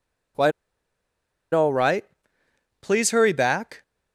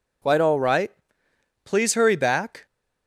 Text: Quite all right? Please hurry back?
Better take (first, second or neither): second